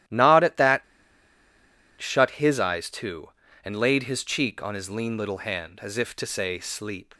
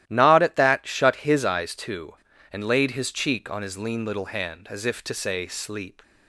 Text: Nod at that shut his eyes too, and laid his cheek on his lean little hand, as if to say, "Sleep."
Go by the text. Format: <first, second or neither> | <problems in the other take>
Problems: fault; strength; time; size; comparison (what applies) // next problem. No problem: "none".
second | starts louder than the rest; strong; until 2.2 s; 13.5 dB; strong in the second // pauses between "that" and "shut"; at 0.8 s; 1.1 s long